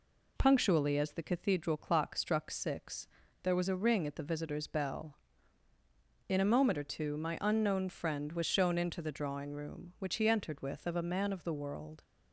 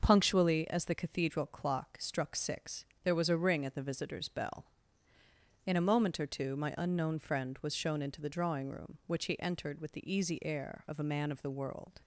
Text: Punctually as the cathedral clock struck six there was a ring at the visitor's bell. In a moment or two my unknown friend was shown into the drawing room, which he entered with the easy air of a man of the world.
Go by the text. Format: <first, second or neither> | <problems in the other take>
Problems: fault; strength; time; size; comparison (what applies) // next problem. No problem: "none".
second | pauses between "six" and "there"; slight; at 3.0 s; 0.34 s long; slight in the second // skips "the easy air"; at 10.8 s